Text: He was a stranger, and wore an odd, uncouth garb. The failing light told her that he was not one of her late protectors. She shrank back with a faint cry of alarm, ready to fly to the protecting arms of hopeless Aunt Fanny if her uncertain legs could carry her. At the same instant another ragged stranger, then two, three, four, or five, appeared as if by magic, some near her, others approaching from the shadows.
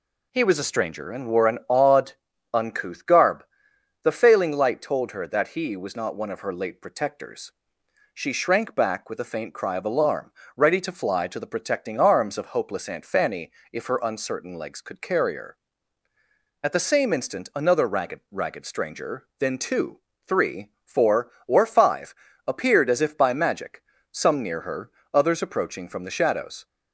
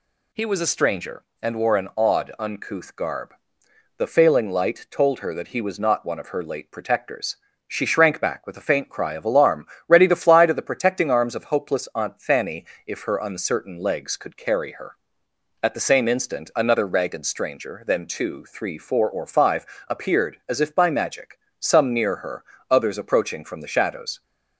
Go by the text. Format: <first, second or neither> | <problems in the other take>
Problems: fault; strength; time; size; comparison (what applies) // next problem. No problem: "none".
second | pauses between "Fanny" and "if"; slight; at 13.5 s; 0.22 s long; slight in the second // says "ragged" twice; at 18.3 s